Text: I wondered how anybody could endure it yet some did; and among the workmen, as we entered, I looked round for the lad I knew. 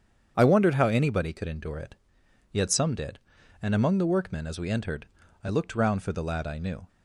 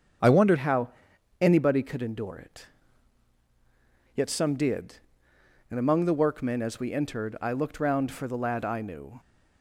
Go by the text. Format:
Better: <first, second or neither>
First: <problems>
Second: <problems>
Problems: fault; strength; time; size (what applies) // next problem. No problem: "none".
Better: first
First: starts louder than the rest; strong; until 1.3 s; 8 dB // pauses between "it" and "yet"; noticeable; at 1.9 s; 0.56 s long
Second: starts louder than the rest; strong; until 1.7 s; 8 dB // changes voice at "how"; from 0.5 s on; 8.6 s long // pauses between "how" and "anybody"; noticeable; at 0.8 s; 0.54 s long // pauses between "it" and "yet"; strong; at 2.6 s; 1.5 s long